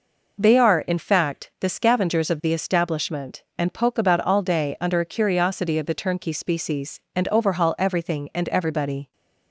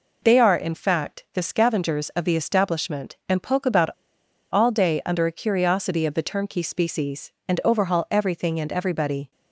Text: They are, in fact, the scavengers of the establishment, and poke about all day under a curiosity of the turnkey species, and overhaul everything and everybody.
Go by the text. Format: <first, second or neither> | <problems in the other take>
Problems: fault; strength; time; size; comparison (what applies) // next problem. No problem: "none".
first | pauses between "about" and "all"; noticeable; at 3.9 s; 0.62 s long